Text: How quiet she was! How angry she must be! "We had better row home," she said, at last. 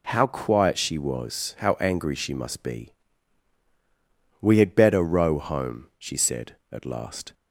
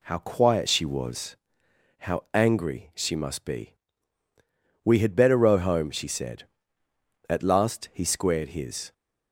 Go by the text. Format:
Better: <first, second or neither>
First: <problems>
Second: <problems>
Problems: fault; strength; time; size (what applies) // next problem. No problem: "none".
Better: first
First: none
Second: goes on to say "He squared his"; noticeable; from 7.9 s on; 1.0 s long